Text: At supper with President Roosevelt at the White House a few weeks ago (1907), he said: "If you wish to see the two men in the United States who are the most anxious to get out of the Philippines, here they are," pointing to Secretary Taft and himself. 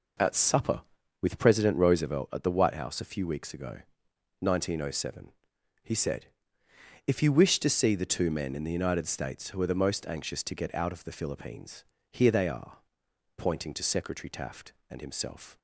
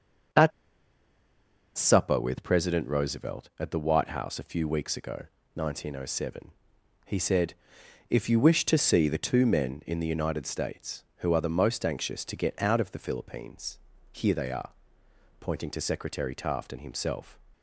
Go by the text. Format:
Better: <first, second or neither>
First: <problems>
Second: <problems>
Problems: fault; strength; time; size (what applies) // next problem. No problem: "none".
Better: first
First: none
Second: starts louder than the rest; until 2.6 s; 7 dB // pauses between "At" and "supper"; strong; at 0.5 s; 1.2 s long